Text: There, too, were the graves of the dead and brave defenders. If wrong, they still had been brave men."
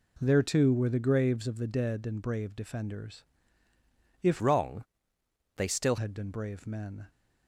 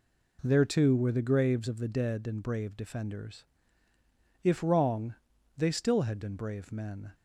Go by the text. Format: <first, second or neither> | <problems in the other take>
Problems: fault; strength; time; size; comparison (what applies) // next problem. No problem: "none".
second | changes voice from "wrong" to "still"; from 4.3 to 5.9 s; 1.6 s long